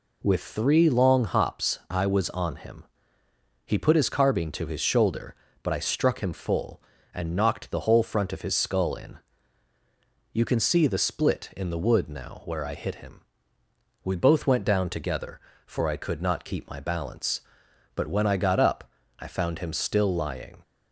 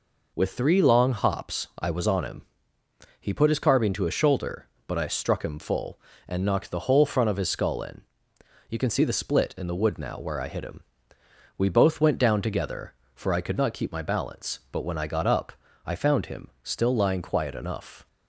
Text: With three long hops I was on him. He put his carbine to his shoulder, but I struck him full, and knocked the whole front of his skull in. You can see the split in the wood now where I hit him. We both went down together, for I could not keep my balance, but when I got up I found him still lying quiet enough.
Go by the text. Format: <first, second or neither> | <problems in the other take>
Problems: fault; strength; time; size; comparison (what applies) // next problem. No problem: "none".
second | pauses between "up" and "I"; slight; at 18.8 s; 0.34 s long; slight in the second // stops before "quiet enough"; at 20.6 s